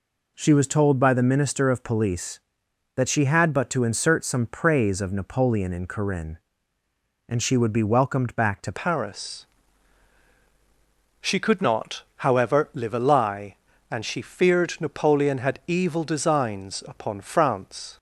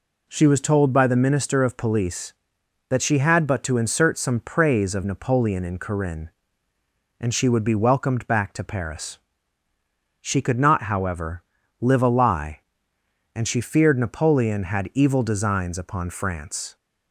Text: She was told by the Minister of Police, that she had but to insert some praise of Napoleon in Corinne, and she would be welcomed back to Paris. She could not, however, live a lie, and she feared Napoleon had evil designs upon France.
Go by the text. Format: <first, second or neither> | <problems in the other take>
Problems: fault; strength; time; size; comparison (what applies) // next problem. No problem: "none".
second | changes voice at "Paris"; from 8.7 s on; 9.2 s long